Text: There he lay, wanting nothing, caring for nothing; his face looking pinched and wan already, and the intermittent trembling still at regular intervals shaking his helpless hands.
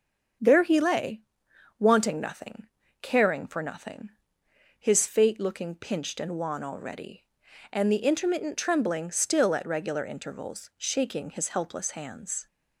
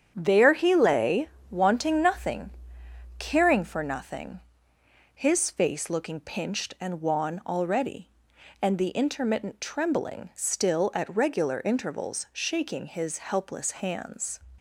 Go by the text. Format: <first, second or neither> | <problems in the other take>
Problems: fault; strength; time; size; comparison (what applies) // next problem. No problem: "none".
second | starts louder than the rest; until 1.9 s; 7 dB; strong in the second // says "fate" for "face"; at 5.0 s